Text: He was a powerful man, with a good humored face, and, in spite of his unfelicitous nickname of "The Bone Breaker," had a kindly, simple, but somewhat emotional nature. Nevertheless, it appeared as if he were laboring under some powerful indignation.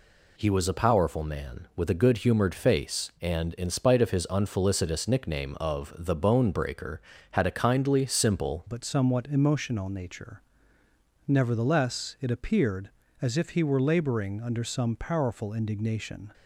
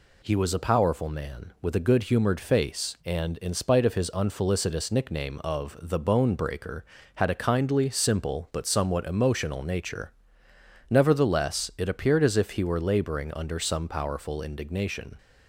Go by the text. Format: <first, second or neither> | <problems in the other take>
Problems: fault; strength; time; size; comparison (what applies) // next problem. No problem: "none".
second | changes voice at "but"; from 8.6 s on; 7.7 s long